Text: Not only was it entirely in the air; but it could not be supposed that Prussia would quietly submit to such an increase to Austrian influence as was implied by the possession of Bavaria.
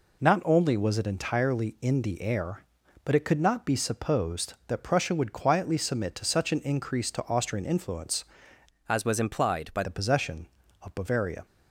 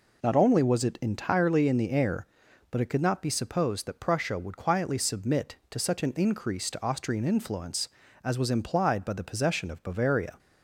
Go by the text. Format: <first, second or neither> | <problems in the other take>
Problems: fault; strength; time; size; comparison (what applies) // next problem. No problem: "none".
second | changes voice from "as" to "by"; from 8.8 to 9.8 s; 1.0 s long